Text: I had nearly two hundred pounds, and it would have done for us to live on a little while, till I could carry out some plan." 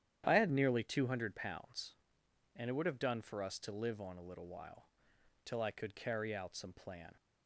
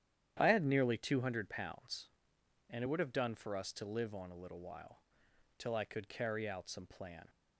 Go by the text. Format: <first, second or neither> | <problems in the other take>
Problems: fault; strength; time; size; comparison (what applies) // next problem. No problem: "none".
neither | starts louder than the rest; strong; the same in both